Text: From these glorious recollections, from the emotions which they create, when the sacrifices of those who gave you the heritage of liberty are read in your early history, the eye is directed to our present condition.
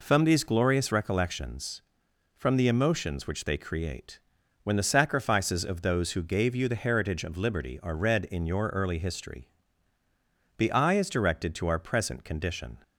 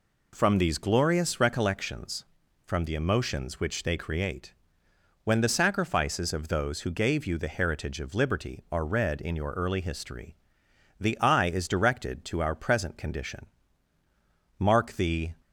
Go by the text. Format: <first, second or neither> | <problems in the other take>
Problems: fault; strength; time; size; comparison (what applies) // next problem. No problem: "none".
first | goes on to say "Mark the"; noticeable; from 14.5 s on; 0.74 s long